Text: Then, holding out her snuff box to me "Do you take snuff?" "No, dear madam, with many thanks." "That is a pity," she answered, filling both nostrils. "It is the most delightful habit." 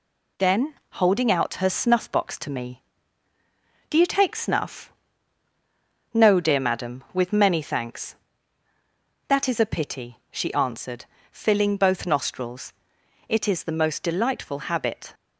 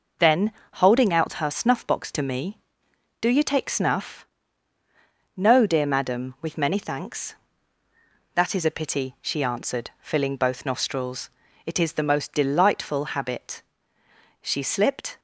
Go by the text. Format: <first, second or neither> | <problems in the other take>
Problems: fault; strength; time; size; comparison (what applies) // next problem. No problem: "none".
first | goes on to say "She slipped"; noticeable; from 14.4 s on; 0.78 s long